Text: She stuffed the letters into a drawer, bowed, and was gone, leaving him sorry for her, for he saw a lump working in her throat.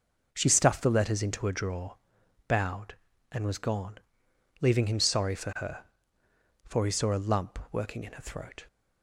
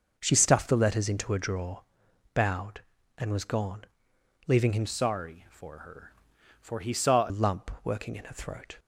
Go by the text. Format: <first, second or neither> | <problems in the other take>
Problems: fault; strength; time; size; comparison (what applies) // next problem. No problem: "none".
first | changes voice from "sorry" to "saw"; from 4.8 to 7.3 s; 2.5 s long